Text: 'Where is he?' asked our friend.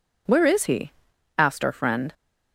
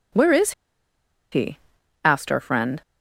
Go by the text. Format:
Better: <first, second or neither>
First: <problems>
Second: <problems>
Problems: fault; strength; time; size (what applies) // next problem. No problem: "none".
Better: first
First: none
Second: pauses between "is" and "he"; noticeable; at 0.5 s; 0.80 s long